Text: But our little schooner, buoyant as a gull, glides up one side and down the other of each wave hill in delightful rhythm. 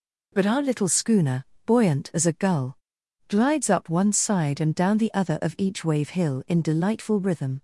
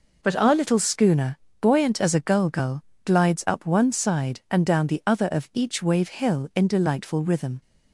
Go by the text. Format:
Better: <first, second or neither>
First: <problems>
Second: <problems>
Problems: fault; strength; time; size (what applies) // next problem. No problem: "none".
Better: first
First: none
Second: says "gull" twice; at 2.4 s